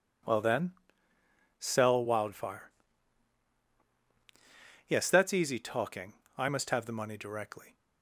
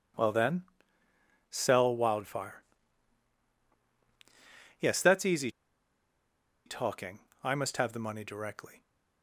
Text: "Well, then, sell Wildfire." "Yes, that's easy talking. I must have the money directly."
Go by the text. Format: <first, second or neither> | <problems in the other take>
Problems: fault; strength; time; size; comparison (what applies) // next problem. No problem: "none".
first | pauses between "easy" and "talking"; at 5.4 s; 1.1 s long